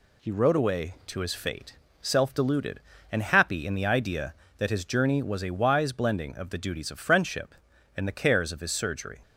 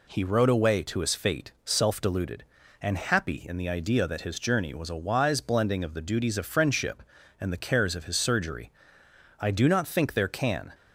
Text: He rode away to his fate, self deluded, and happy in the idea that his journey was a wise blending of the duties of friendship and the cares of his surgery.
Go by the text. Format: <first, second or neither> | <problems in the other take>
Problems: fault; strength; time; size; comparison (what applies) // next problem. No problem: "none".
first | goes on to say "I do not think there can"; from 9.3 s on; 1.3 s long